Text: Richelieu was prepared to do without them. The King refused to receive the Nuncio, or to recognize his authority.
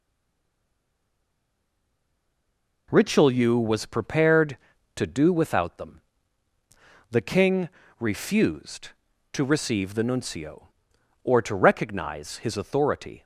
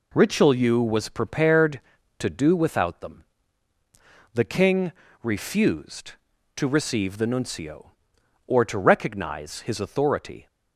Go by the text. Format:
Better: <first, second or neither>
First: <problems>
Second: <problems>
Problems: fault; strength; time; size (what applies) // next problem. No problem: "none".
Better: second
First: stays silent before the first word; strong; until 2.8 s; 2.8 s long // pauses between "King" and "refused"; slight; at 7.6 s; 0.30 s long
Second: pauses between "King" and "refused"; slight; at 4.9 s; 0.30 s long